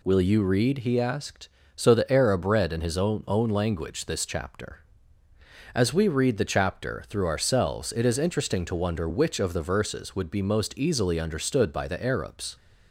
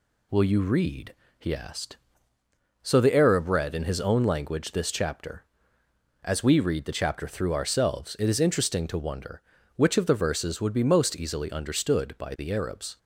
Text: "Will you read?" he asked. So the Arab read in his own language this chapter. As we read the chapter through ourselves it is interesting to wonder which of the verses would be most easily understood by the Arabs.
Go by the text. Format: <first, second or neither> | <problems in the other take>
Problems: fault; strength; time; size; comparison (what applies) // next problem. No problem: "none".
second | says "own" twice; at 3.2 s